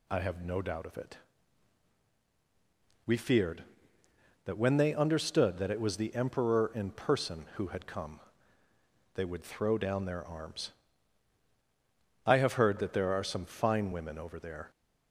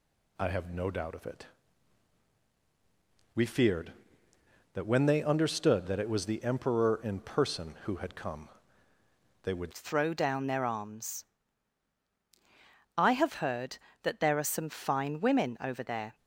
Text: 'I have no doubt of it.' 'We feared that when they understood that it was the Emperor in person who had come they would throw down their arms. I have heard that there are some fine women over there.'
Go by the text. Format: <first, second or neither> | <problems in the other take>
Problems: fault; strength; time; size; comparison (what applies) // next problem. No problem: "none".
first | pauses between "come" and "they"; noticeable; at 8.4 s; 0.96 s long; noticeable in the first // changes voice at "throw"; from 9.7 s on; 6.4 s long